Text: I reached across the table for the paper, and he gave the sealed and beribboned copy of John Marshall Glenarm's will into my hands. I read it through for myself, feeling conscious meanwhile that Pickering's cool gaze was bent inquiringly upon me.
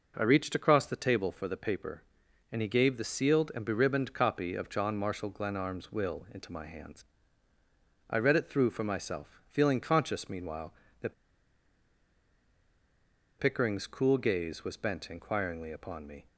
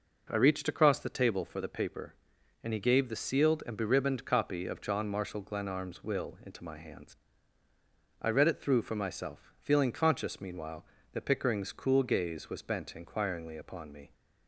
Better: second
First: pauses between "that" and "Pickering's"; strong; at 11.1 s; 2.2 s long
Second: none

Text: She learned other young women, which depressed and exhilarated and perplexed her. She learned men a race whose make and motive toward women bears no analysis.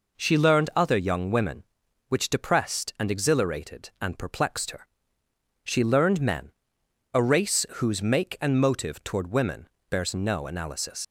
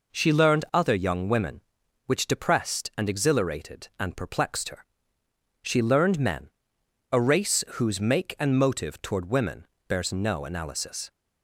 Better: second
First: pauses between "men" and "a"; noticeable; at 6.5 s; 0.66 s long // pauses between "women" and "bears"; slight; at 9.6 s; 0.20 s long // leaves "analysis" unfinished; at 11.0 s; 95 ms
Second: pauses between "men" and "a"; noticeable; at 6.4 s; 0.66 s long // pauses between "women" and "bears"; slight; at 9.6 s; 0.20 s long

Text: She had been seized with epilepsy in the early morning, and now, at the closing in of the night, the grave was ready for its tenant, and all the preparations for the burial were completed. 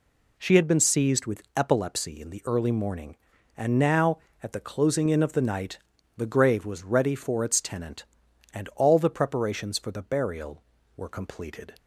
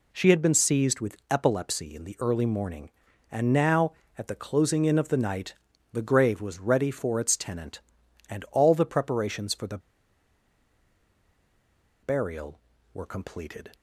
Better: first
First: none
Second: pauses between "the" and "burial"; strong; at 9.7 s; 2.2 s long

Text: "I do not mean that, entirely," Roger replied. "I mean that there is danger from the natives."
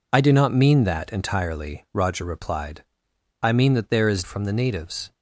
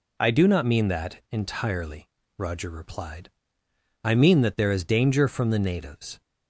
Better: second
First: skips "danger"; at 4.2 s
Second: none

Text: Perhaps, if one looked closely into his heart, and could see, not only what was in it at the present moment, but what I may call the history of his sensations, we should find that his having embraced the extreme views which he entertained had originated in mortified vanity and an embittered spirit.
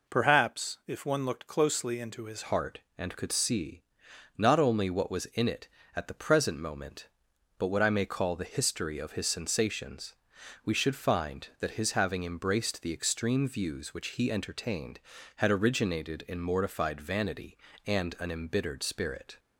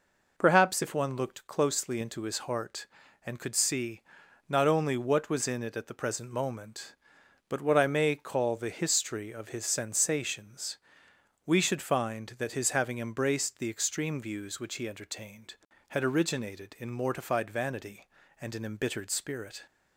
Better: second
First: changes voice at "heart"; from 2.4 s on; 16.9 s long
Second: none

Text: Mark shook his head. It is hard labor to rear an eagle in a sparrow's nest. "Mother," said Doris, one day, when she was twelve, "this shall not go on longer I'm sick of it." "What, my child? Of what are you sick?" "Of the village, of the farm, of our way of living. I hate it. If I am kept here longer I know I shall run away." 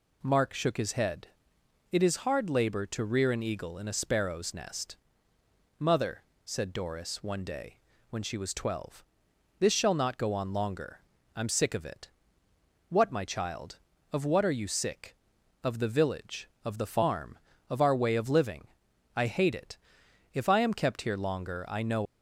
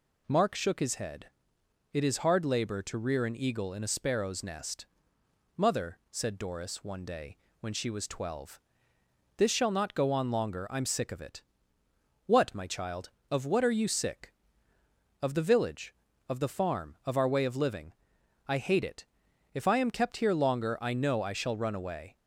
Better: second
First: pauses between "longer" and "I'm"; slight; at 10.9 s; 0.34 s long // stops before "I shall run away"; at 22.0 s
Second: none

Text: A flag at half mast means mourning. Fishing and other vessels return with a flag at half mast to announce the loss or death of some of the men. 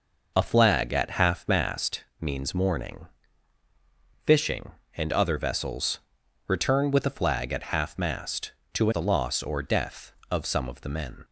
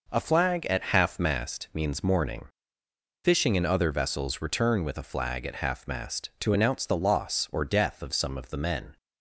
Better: second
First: pauses between "mast" and "means"; slight; at 2.0 s; 0.18 s long // pauses between "vessels" and "return"; noticeable; at 5.9 s; 0.48 s long // skips "announce"; at 8.9 s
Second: none

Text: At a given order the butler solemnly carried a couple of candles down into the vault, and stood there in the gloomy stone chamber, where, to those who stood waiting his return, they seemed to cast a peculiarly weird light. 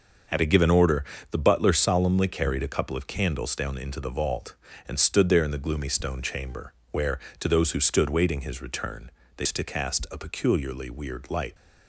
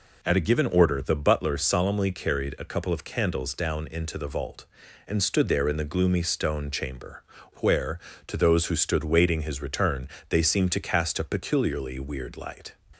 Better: second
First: starts louder than the rest; until 1.5 s; 6 dB // pauses between "order" and "the"; slight; at 1.0 s; 0.26 s long // skips "seemed"; at 9.4 s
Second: none

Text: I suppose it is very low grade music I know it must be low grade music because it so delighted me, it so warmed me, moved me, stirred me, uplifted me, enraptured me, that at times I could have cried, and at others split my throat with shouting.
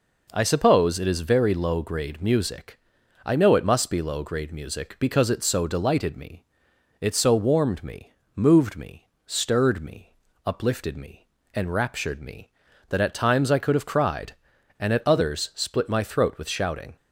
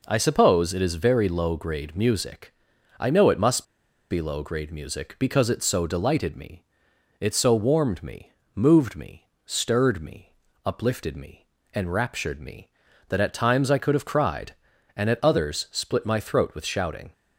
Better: first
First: pauses between "music" and "I"; noticeable; at 2.7 s; 0.46 s long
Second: pauses between "music" and "I"; noticeable; at 2.5 s; 0.46 s long // pauses between "must" and "be"; noticeable; at 3.6 s; 0.47 s long

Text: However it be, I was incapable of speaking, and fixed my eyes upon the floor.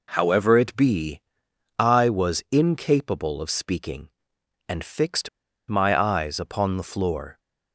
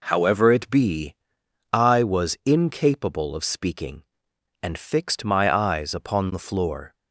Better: second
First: pauses between "fixed" and "my"; at 5.2 s; 0.39 s long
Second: none

